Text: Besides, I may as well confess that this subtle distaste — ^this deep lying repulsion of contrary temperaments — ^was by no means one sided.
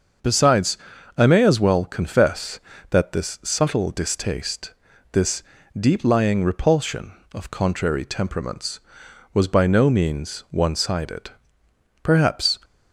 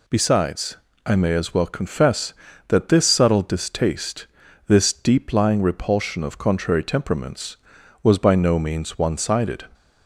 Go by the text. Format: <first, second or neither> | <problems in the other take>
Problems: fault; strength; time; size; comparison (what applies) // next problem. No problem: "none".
second | starts louder than the rest; until 1.6 s; 6.5 dB // pauses between "this" and "deep"; slight; at 5.4 s; 0.36 s long // goes on to say "Perhaps"; from 12.0 s on; 0.56 s long